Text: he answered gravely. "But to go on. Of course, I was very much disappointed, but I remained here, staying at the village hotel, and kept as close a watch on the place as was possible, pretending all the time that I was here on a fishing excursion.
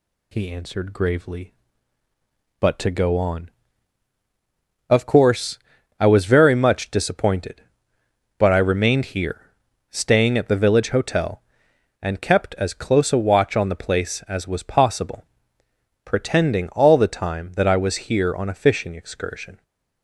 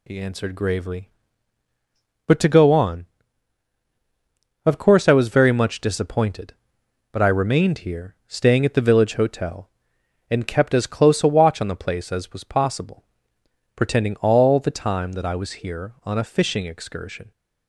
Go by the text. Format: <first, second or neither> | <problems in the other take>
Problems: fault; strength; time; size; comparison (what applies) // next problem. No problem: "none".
neither | none